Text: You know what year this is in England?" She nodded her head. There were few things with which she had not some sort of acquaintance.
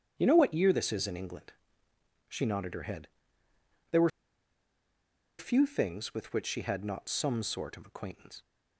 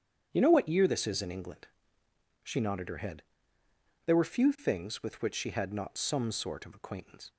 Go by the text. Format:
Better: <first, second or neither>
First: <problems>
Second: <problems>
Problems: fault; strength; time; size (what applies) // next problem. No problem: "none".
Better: second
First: starts louder than the rest; strong; until 1.1 s; 8.5 dB // pauses between "were" and "few"; strong; at 4.0 s; 1.3 s long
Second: starts louder than the rest; strong; until 1.3 s; 8.5 dB